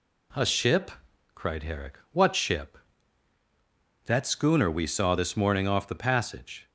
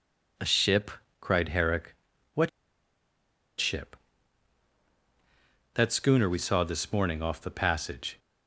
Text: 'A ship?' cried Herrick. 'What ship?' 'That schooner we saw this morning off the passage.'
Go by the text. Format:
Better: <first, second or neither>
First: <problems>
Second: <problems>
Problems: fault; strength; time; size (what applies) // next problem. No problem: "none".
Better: first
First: none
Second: pauses between "What" and "ship"; at 2.4 s; 1.1 s long